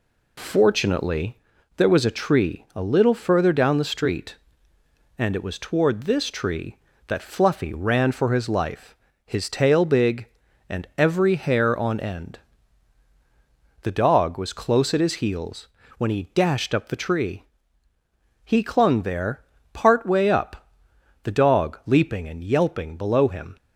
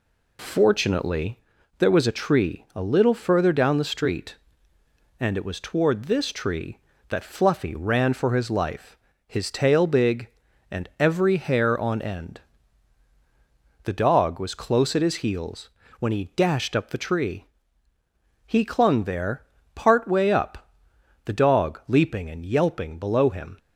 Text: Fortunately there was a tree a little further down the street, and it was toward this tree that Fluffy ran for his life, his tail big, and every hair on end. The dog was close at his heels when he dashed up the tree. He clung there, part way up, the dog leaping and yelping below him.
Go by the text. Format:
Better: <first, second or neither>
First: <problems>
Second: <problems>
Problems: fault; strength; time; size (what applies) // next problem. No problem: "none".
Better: neither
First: pauses between "Fortunately" and "there"; at 1.3 s; 0.40 s long // pauses between "heels" and "when"; slight; at 15.6 s; 0.30 s long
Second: pauses between "Fortunately" and "there"; at 1.3 s; 0.40 s long // pauses between "heels" and "when"; slight; at 15.6 s; 0.30 s long